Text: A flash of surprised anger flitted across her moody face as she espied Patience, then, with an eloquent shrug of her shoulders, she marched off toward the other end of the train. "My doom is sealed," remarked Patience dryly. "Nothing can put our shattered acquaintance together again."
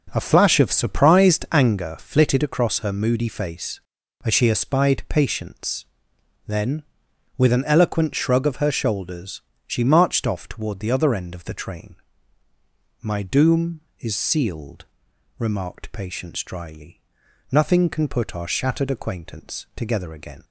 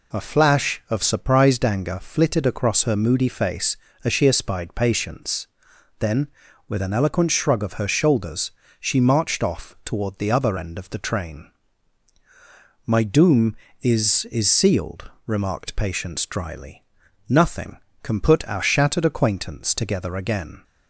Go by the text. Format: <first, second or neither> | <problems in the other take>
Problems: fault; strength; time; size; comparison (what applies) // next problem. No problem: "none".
first | says "is" twice; at 14.3 s